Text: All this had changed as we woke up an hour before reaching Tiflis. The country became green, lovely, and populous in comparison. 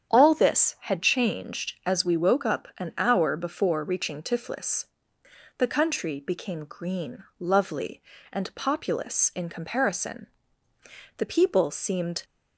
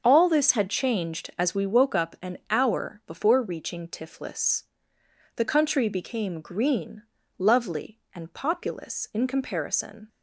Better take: second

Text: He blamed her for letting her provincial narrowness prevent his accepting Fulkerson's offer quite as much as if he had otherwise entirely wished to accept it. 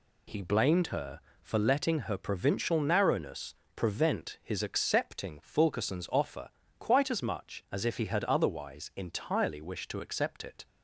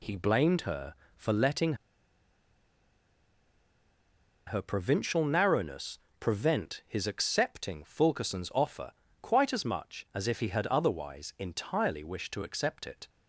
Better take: first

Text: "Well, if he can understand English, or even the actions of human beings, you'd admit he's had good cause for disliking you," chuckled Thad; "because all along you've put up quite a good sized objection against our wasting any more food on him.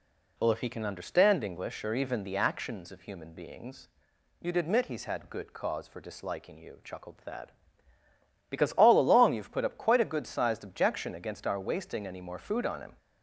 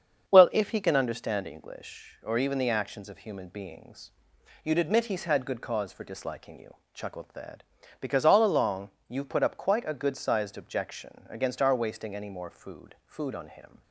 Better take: first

